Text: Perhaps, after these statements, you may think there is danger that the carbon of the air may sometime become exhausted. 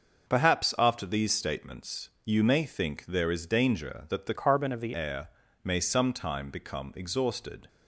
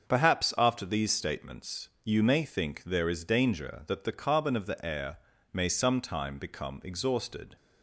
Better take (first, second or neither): second